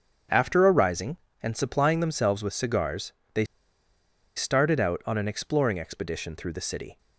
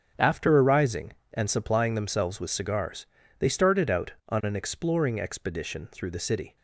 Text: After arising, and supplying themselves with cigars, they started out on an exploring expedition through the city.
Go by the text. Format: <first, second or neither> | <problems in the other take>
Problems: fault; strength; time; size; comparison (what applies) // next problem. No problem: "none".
second | starts louder than the rest; strong; until 1.5 s; 7.5 dB; strong in the second // pauses between "they" and "started"; noticeable; at 3.4 s; 0.90 s long